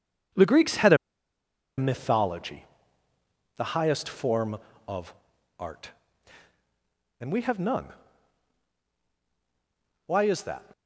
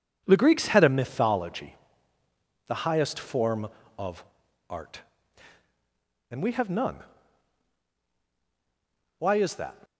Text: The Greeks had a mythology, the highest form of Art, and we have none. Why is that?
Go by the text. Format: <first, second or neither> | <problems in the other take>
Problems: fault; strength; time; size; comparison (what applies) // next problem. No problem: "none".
second | pauses between "a" and "mythology"; noticeable; at 0.9 s; 0.81 s long // pauses between "of" and "Art"; noticeable; at 5.1 s; 0.46 s long; noticeable in the second